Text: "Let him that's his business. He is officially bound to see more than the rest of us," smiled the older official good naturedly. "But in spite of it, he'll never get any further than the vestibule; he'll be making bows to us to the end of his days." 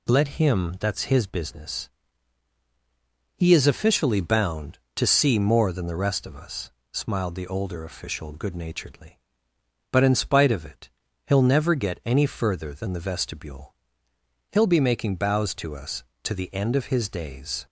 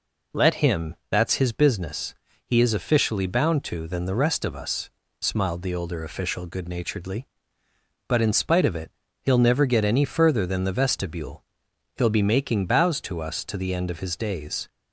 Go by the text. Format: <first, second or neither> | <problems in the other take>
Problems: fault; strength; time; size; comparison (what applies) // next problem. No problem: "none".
first | skips "see more"; at 3.8 s